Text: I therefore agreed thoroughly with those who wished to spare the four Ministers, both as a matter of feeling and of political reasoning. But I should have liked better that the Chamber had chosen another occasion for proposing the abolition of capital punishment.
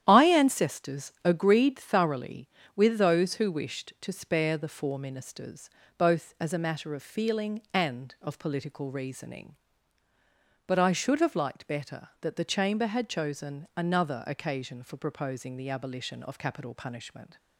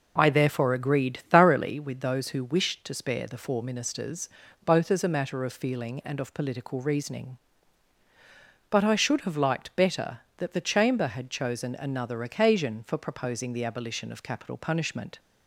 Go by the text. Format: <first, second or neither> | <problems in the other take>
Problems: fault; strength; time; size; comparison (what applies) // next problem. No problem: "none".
second | starts louder than the rest; strong; until 1.0 s; 10.5 dB // says "ancestors" for "therefore"; at 0.2 s